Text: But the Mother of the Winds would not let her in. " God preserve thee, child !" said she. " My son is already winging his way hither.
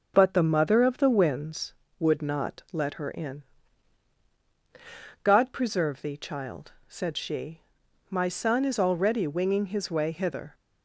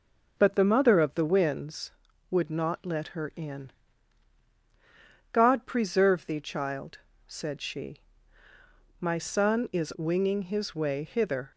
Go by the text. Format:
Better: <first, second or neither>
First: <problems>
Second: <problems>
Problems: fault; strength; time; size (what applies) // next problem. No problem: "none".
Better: first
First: none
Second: skips "already"; at 9.9 s